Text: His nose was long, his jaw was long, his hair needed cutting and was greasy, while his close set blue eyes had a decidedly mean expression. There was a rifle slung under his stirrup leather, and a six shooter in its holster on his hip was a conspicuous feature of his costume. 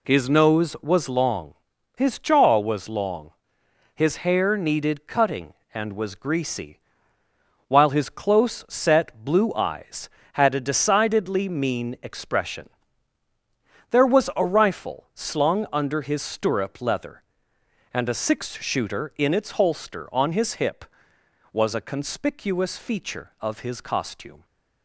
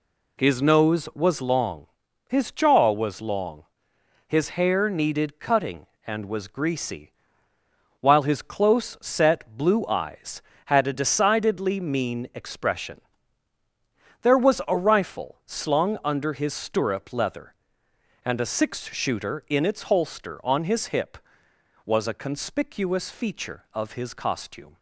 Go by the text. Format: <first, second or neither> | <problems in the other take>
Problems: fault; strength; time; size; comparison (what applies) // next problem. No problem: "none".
neither | none